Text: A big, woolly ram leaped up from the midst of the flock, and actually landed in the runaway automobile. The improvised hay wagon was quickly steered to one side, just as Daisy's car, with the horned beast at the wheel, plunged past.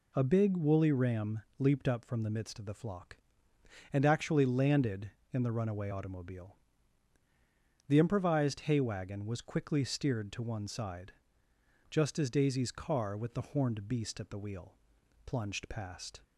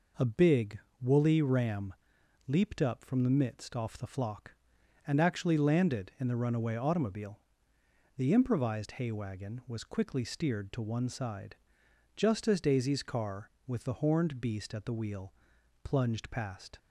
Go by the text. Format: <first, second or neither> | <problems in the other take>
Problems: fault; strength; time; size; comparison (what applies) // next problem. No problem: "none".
first | pauses between "ram" and "leaped"; noticeable; at 1.9 s; 0.54 s long; slight in the first // says "off" for "of"; at 3.7 s